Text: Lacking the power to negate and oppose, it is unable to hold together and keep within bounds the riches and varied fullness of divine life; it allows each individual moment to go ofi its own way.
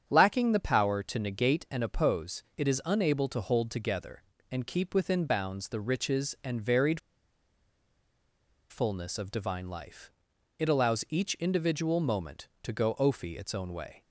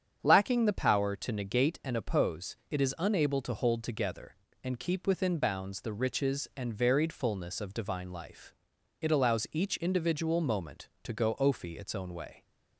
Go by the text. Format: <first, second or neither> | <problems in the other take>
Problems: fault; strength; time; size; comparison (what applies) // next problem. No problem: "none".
second | starts louder than the rest; strong; until 1.0 s; 8 dB; strong in the second // pauses between "varied" and "fullness"; strong; at 6.9 s; 1.7 s long